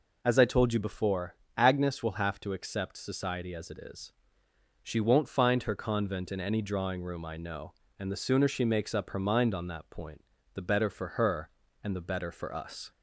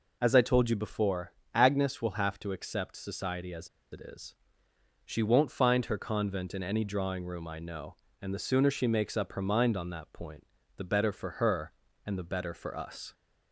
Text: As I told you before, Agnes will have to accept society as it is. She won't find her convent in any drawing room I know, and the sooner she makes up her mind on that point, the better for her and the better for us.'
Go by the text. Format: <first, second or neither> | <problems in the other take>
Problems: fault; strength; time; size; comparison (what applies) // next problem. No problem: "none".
first | pauses between "as" and "it"; slight; at 3.6 s; 0.23 s long